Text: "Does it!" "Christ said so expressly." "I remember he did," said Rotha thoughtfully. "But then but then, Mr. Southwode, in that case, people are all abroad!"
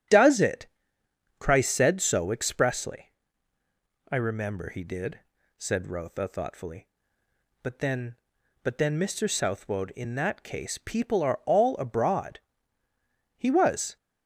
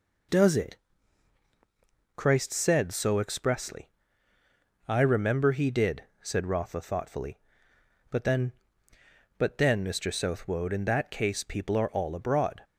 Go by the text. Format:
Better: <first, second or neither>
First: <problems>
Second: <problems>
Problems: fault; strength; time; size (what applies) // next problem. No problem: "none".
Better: second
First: starts louder than the rest; strong; until 1.8 s; 9.5 dB // goes on to say "He was"; from 13.3 s on; 0.60 s long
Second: none